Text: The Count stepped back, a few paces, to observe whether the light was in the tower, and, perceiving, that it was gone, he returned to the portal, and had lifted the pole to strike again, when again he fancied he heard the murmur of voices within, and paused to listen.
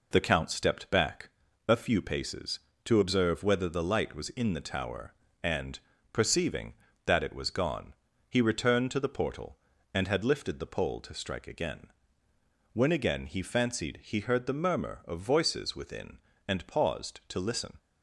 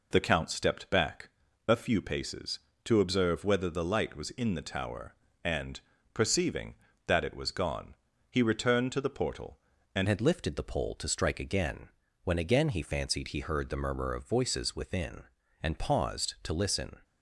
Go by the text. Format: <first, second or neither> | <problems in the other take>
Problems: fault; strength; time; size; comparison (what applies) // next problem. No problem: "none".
first | changes voice at "had"; from 10.0 s on; 6.9 s long